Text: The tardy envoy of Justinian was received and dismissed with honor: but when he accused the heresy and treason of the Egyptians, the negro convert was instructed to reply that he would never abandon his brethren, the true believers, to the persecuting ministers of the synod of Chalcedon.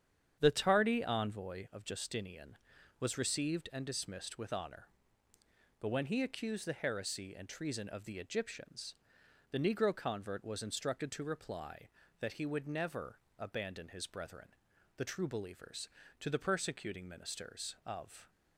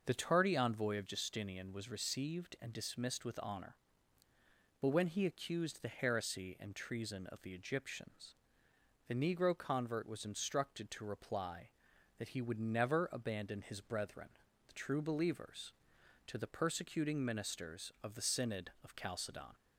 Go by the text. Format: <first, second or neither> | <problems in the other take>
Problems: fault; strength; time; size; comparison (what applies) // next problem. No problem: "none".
second | starts louder than the rest; strong; until 1.4 s; 8.5 dB // pauses between "never" and "abandon"; slight; at 13.1 s; 0.18 s long // stops before "the synod of Chalcedon"; at 18.2 s